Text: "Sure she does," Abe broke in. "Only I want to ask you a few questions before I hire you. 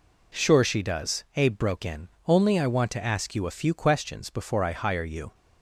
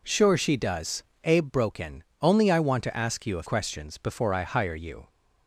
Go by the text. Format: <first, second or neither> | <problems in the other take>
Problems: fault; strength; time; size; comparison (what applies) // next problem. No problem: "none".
first | skips "few"; at 3.4 s